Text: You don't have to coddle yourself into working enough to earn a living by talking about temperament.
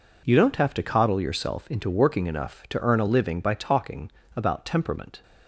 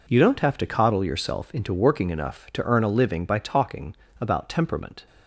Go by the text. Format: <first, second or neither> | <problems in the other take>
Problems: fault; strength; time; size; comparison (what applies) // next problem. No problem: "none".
neither | pauses between "talking" and "about"; slight; the same in both